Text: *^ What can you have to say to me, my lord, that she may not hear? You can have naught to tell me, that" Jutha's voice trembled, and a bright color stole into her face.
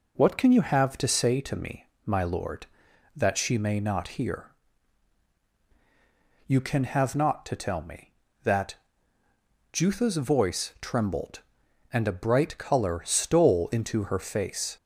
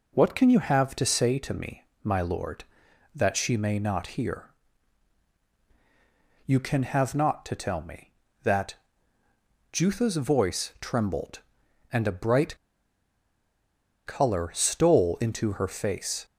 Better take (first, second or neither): first